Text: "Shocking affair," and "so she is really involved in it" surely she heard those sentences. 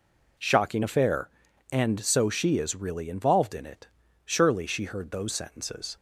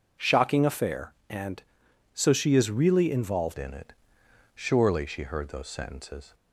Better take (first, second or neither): first